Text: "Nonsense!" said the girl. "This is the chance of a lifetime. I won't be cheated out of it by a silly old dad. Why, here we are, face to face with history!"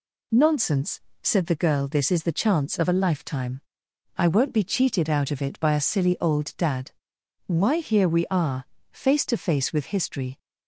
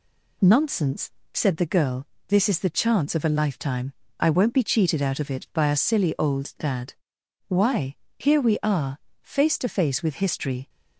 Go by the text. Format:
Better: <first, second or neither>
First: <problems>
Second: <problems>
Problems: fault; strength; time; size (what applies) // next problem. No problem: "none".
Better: neither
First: none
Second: none